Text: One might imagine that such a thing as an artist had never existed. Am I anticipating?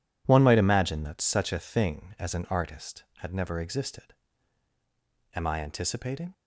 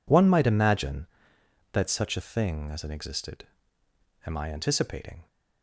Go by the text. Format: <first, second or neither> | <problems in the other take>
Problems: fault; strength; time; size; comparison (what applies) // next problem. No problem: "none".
first | skips "artist had never"; at 2.9 s